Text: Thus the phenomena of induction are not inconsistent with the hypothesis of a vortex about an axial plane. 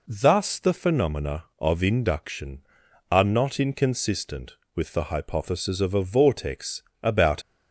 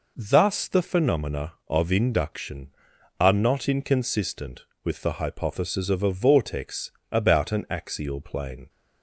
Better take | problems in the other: second | pauses between "vortex" and "about"; slight; at 6.8 s; 0.18 s long; slight in the second // stops before "an axial plane"; at 7.4 s

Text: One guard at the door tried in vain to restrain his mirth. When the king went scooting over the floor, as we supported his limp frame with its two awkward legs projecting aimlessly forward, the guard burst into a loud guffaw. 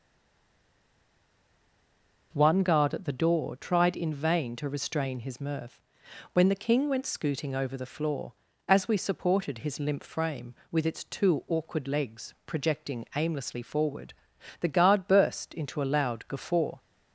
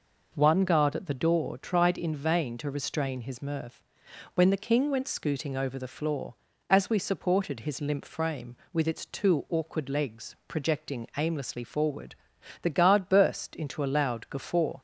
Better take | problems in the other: second | stays silent before the first word; until 2.3 s; 2.3 s long

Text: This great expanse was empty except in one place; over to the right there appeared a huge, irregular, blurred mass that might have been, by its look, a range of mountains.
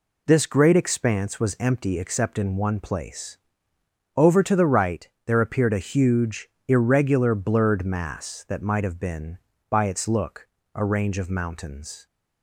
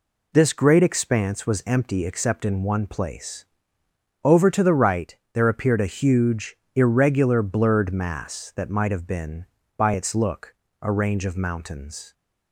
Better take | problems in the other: neither | pauses between "right" and "there"; slight; the same in both

